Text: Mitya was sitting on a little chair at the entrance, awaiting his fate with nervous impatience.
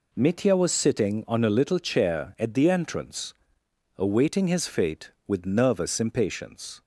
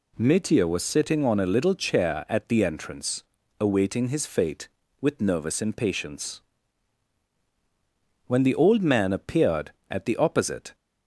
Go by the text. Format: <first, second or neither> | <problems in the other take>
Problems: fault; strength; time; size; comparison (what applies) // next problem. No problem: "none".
first | goes on to say "When the old man appeared at the opposite"; strong; from 8.2 s on; 2.4 s long